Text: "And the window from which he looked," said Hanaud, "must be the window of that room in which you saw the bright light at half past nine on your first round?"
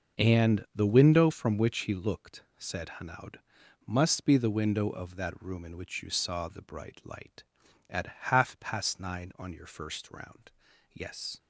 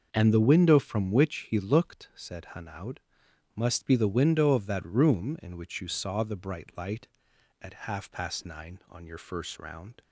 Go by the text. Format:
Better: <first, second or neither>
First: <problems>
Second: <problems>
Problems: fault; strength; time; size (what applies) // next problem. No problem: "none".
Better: second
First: starts louder than the rest; until 1.2 s; 6 dB // goes on to say "Yes"; slight; from 10.9 s on; 0.48 s long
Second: starts louder than the rest; noticeable; until 1.1 s; 6 dB